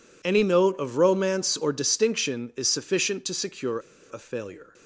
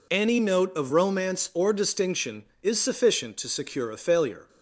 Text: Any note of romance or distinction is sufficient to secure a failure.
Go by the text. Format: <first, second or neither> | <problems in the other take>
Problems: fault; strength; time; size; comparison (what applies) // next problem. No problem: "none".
second | pauses between "secure" and "a"; slight; at 3.7 s; 0.29 s long